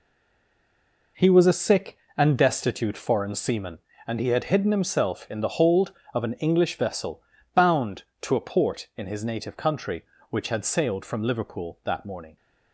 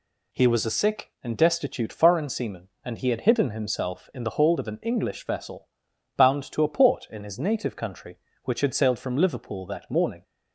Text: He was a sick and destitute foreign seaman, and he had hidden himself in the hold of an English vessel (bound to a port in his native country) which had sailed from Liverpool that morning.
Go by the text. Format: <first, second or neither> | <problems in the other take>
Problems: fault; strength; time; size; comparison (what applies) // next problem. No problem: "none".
second | stays silent before the first word; until 1.1 s; 1.1 s long